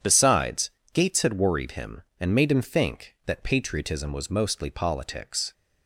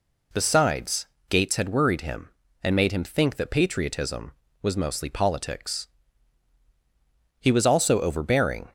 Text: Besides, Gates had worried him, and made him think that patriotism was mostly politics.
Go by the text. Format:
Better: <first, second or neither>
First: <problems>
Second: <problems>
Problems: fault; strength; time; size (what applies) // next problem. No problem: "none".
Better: first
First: none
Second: goes on to say "He was also overbearing"; from 7.3 s on; 1.3 s long